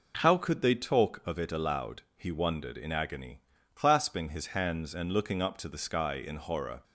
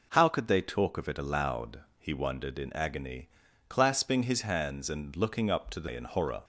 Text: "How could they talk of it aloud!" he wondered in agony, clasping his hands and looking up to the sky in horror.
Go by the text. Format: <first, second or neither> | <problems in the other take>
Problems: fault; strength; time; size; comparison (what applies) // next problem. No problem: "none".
first | skips "sky"; at 5.8 s